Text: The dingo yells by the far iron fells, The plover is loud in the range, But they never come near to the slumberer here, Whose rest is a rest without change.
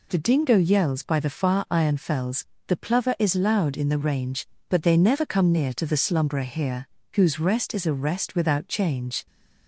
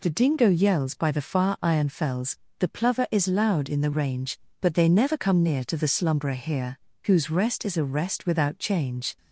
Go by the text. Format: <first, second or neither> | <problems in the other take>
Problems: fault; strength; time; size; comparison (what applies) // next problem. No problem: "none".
neither | none